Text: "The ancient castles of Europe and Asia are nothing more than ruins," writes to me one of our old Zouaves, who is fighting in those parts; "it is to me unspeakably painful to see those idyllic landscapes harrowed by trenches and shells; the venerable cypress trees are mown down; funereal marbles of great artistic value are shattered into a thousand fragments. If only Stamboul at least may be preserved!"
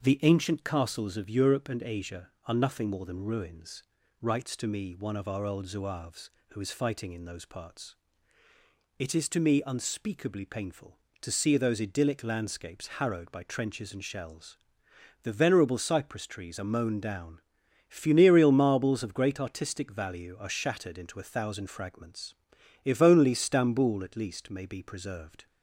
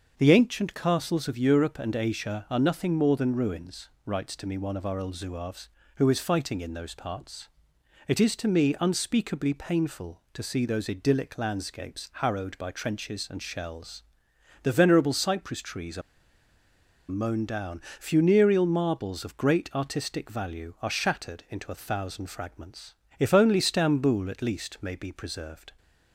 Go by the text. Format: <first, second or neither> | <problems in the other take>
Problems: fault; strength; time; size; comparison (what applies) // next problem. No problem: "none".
first | starts louder than the rest; until 1.1 s; 6.5 dB; also in the first // pauses between "are" and "mown"; at 16.0 s; 1.0 s long